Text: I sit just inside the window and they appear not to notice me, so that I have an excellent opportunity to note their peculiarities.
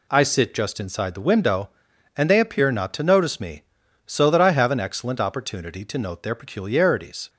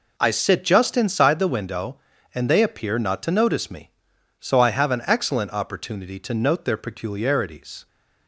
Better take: first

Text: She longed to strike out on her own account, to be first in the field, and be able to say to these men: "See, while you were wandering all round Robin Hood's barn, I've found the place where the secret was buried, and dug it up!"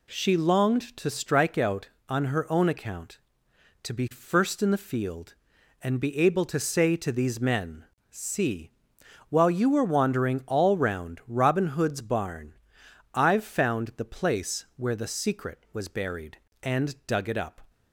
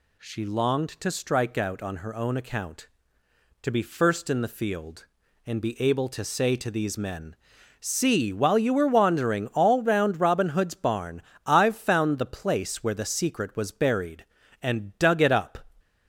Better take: neither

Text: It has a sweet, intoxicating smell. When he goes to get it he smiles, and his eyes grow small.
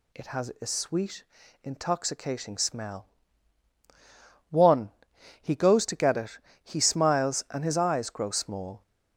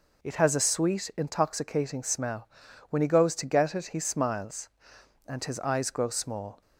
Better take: second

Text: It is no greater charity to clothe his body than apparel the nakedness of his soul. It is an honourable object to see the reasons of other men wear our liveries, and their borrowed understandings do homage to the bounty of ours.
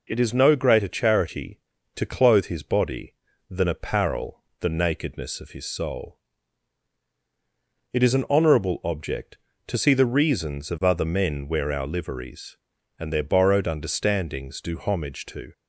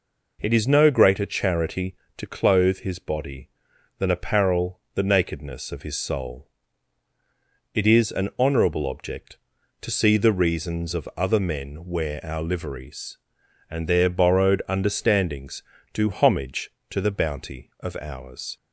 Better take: second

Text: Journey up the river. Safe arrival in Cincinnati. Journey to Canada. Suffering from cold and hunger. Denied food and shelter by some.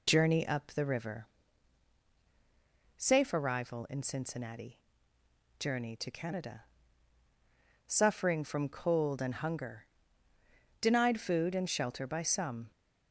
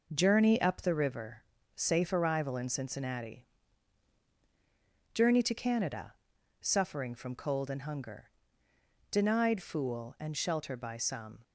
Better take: first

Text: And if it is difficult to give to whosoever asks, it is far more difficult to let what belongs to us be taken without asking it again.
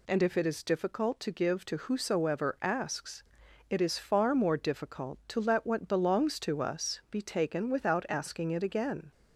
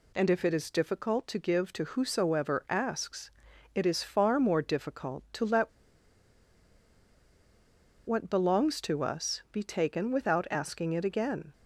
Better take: first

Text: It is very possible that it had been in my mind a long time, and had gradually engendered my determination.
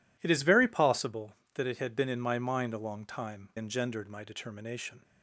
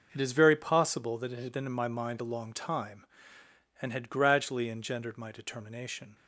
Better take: second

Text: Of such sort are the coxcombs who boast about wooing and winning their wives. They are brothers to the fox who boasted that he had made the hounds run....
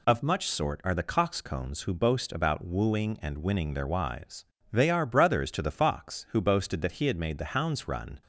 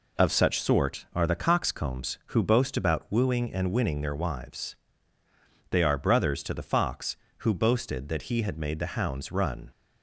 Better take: second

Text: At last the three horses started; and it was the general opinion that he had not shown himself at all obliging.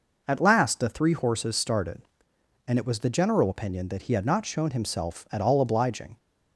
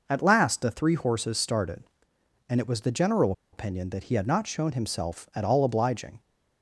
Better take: first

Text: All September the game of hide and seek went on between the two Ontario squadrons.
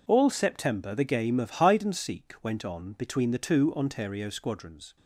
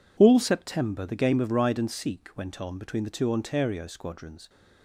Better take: first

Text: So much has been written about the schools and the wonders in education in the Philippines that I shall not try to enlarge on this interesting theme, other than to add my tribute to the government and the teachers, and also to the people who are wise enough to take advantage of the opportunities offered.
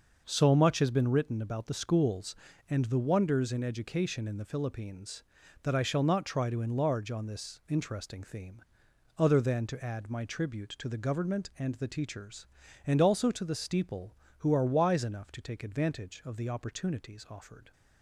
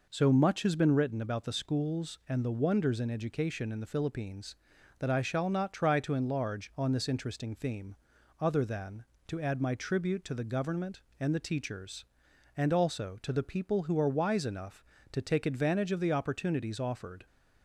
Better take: second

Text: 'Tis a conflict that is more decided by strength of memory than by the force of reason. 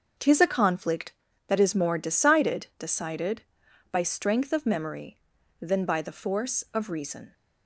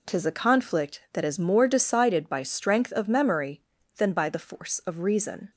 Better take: second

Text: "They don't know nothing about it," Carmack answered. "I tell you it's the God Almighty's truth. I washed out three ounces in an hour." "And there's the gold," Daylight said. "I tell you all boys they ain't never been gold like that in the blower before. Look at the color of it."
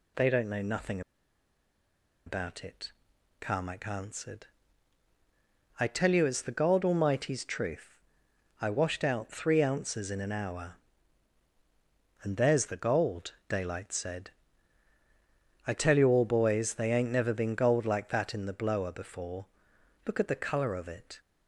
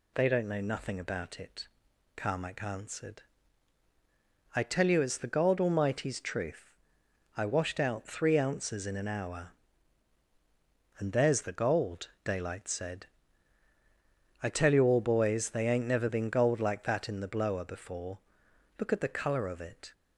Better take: second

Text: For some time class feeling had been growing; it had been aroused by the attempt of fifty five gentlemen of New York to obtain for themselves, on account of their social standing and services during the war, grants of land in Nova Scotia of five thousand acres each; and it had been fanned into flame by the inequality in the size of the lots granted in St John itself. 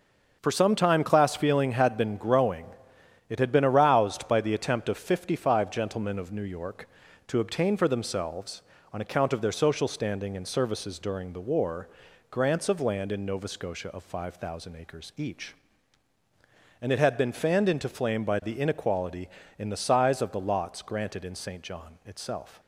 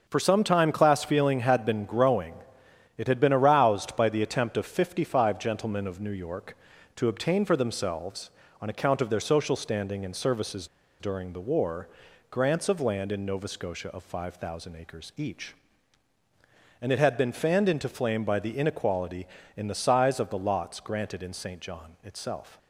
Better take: first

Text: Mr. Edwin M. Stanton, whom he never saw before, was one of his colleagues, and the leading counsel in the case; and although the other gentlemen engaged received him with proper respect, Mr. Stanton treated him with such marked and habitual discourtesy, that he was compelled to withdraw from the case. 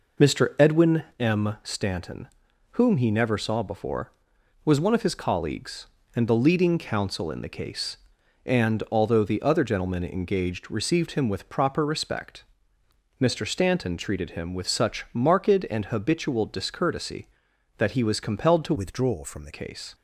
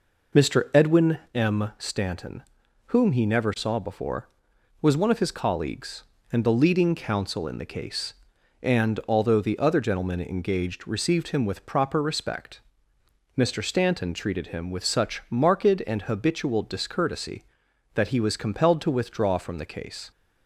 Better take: second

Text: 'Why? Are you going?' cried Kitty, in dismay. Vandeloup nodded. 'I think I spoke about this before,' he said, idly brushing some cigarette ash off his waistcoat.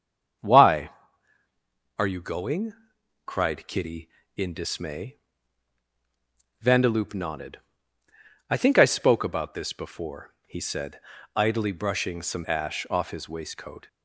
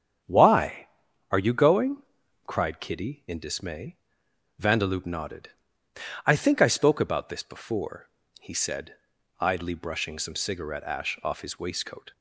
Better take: second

